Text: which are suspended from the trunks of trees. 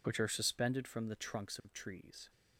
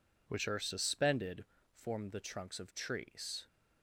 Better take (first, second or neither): first